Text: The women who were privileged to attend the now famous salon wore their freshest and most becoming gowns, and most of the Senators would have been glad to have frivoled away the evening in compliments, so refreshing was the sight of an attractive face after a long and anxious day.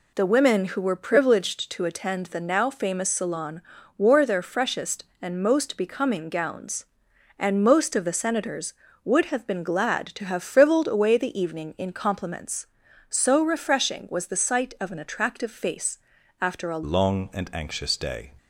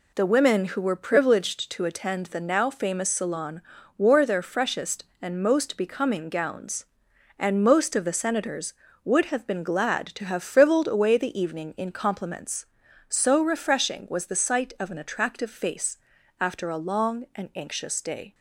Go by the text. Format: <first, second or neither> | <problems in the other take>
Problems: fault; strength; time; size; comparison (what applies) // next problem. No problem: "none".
second | pauses between "salon" and "wore"; slight; at 3.6 s; 0.36 s long; slight in the second // pauses between "face" and "after"; at 15.9 s; 0.42 s long; also in the second // changes voice at "long"; from 16.8 s on; 1.5 s long